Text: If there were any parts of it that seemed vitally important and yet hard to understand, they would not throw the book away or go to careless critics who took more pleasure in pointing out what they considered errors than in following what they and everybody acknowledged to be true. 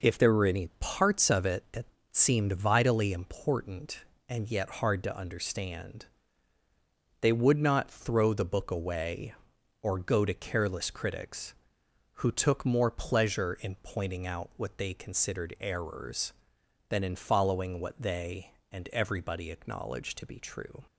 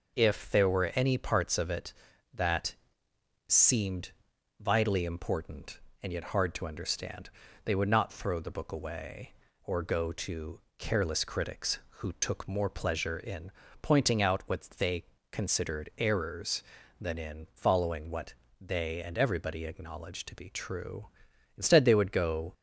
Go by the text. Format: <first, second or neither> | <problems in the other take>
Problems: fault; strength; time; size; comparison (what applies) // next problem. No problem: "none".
first | pauses between "that" and "seemed"; noticeable; at 2.7 s; 0.72 s long; slight in the first // pauses between "seemed" and "vitally"; noticeable; at 4.1 s; 0.48 s long // pauses between "to" and "careless"; slight; at 10.5 s; 0.18 s long // pauses between "in" and "pointing"; slight; at 13.5 s; 0.32 s long // pauses between "they" and "considered"; slight; at 15.0 s; 0.26 s long // pauses between "what" and "they"; slight; at 18.3 s; 0.26 s long // goes on to say "Instead they would go"; noticeable; from 21.6 s on; 0.92 s long